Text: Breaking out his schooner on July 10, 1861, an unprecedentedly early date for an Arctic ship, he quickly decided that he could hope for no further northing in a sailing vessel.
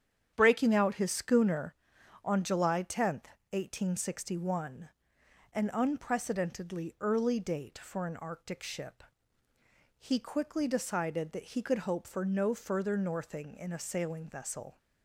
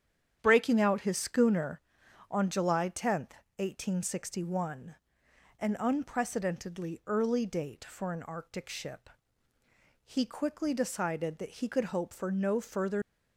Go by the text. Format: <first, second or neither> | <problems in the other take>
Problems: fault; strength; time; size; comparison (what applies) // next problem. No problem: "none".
first | starts louder than the rest; strong; until 1.4 s; 9 dB; strong in the first // stops before "northing in a sailing vessel"; at 13.0 s